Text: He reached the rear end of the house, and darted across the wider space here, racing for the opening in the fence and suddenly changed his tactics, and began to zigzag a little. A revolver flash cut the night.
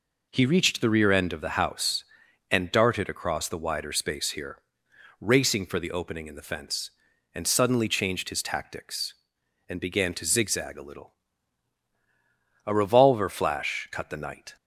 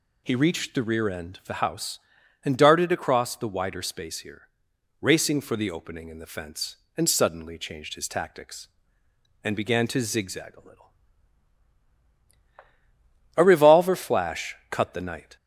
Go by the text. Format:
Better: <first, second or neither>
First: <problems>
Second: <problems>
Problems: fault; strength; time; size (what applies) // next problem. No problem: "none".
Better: neither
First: none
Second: none